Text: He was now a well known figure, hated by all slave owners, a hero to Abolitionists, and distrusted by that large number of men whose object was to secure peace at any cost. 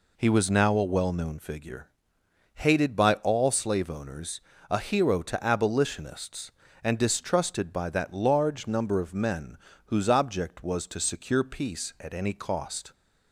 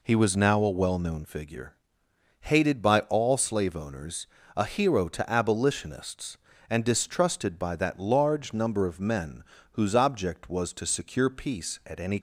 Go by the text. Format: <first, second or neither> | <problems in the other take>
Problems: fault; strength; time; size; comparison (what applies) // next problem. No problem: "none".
first | pauses between "men" and "whose"; slight; at 9.4 s; 0.28 s long; slight in the first // stops before "cost"; at 12.1 s